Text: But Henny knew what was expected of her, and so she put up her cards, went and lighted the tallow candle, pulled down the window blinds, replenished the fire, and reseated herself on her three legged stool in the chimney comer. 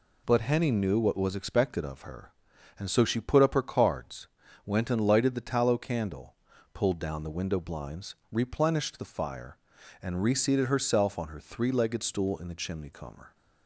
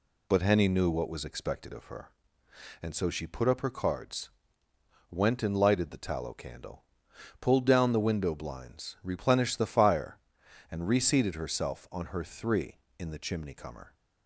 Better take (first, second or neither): first